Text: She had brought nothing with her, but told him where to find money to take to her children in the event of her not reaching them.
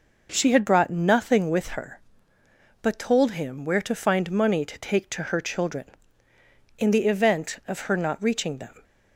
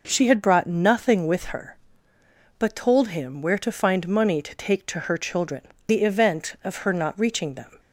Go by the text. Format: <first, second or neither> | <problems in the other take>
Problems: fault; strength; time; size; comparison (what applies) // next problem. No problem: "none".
first | skips "in"; at 5.7 s